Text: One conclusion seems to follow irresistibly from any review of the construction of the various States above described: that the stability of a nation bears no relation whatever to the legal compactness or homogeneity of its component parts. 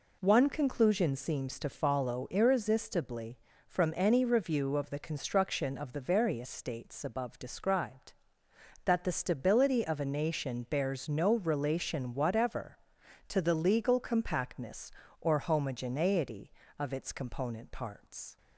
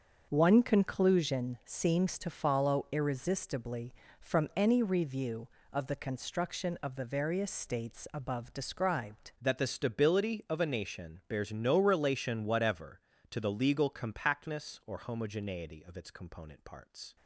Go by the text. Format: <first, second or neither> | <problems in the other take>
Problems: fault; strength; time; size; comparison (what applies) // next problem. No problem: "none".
first | starts louder than the rest; until 1.3 s; 6.5 dB // changes voice at "that"; from 9.4 s on; 7.7 s long